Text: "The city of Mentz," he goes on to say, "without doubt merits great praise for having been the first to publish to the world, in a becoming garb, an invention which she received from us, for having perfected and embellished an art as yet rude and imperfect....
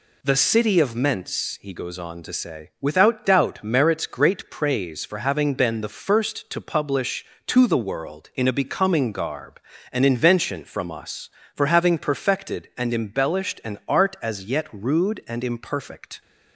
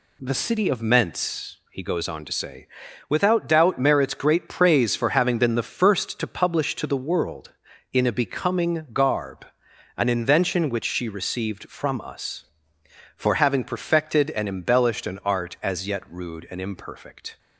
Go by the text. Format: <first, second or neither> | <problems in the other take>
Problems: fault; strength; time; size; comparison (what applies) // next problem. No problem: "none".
second | skips "which she received"; at 10.6 s